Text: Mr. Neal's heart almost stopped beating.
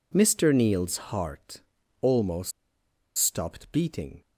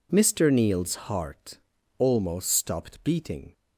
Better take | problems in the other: second | pauses between "heart" and "almost"; at 1.6 s; 0.40 s long; also in the second // pauses between "almost" and "stopped"; noticeable; at 2.5 s; 0.65 s long

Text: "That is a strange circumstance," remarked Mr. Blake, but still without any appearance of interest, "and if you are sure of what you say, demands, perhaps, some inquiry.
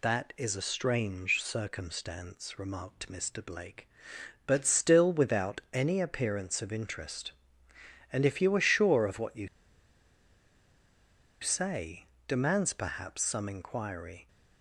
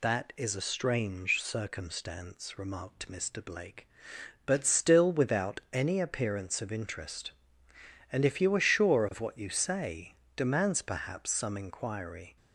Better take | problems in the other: second | pauses between "you" and "say"; strong; at 9.4 s; 1.9 s long

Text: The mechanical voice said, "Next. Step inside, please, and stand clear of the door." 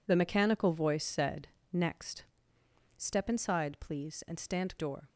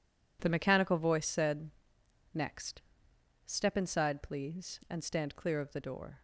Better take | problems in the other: second | skips "clear of the"; at 4.7 s

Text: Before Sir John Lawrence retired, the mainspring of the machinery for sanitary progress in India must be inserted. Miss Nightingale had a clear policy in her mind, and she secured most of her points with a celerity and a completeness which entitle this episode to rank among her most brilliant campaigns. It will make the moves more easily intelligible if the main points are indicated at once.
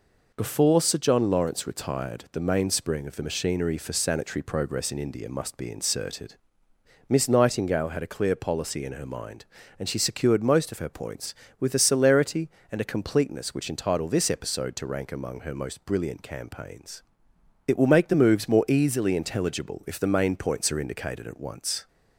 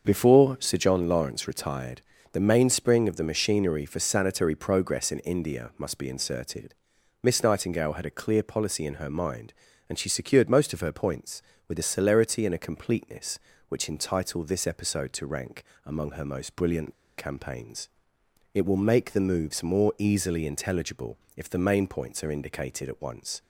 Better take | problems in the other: first | starts louder than the rest; until 1.1 s; 6.5 dB // pauses between "rank" and "among"; slight; at 15.6 s; 0.20 s long // pauses between "brilliant" and "campaigns"; slight; at 16.9 s; 0.26 s long // pauses between "intelligible" and "if"; slight; at 21.1 s; 0.16 s long

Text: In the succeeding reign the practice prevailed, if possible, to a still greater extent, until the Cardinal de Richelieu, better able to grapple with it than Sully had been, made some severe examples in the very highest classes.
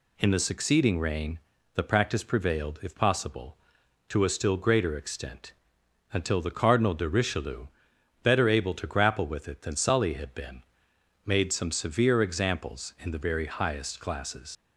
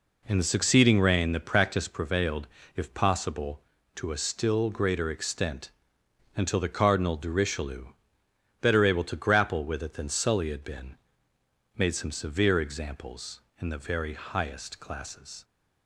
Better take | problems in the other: second | pauses between "reign" and "the"; slight; at 1.3 s; 0.34 s long // leaves "classes" unfinished; at 14.5 s; 85 ms

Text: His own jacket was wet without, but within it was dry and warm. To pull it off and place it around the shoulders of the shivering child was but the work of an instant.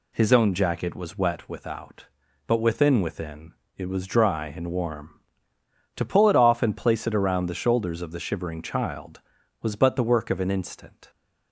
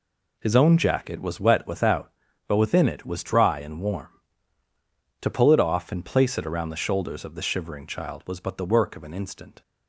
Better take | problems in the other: second | says "within" twice; at 2.9 s

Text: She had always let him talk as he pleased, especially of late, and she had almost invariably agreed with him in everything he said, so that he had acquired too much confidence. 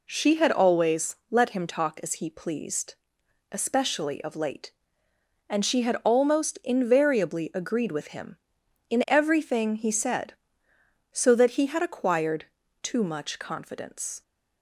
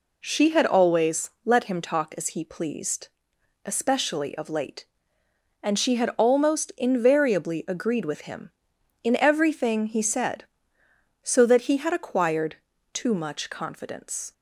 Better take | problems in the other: neither | pauses between "acquired" and "too"; slight; the same in both

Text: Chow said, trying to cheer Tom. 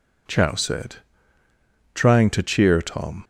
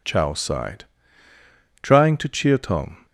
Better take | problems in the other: first | says "sighed" for "said"; at 0.3 s

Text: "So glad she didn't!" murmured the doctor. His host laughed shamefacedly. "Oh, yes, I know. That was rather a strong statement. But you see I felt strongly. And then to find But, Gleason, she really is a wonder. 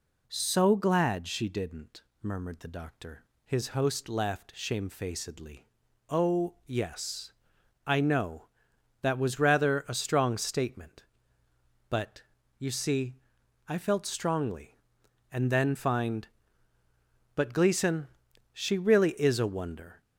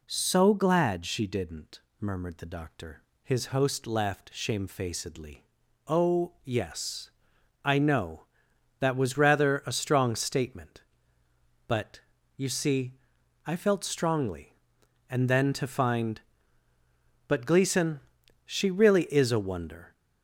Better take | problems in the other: second | pauses between "But" and "you"; slight; at 12.2 s; 0.34 s long; slight in the second // pauses between "see" and "I"; noticeable; at 13.1 s; 0.52 s long; noticeable in the second // skips "to"; at 15.7 s

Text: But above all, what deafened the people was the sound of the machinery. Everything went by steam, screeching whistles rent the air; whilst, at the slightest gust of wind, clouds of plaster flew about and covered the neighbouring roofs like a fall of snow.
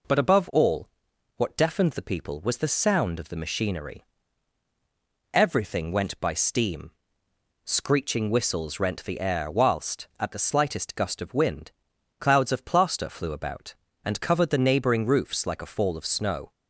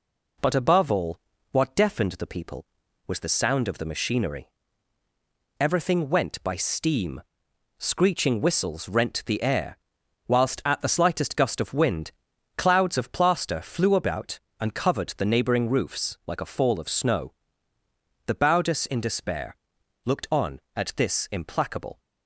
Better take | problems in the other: first | goes on to say "The Baudus in despair looked on at this implacable"; strong; from 18.2 s on; 3.7 s long

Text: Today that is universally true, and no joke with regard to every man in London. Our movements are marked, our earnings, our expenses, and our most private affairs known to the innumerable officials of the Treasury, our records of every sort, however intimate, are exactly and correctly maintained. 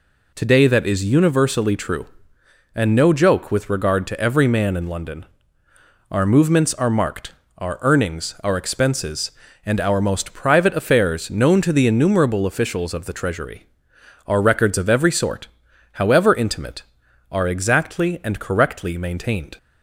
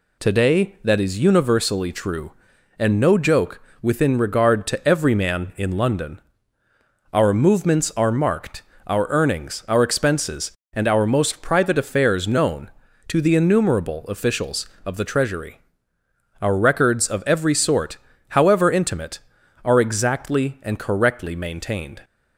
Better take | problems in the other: first | says "within" for "with"; at 3.8 s

